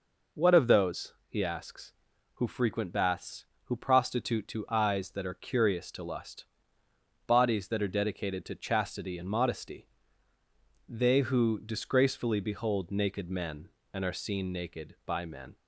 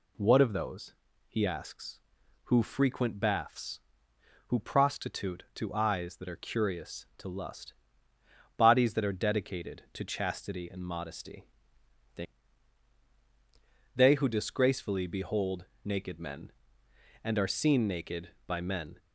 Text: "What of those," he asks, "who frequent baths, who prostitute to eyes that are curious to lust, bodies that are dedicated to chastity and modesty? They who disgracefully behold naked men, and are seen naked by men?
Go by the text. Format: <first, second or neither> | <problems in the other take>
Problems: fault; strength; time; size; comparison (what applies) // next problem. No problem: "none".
first | says "They" twice; at 13.9 s // pauses between "behold" and "naked"; slight; at 15.6 s; 0.18 s long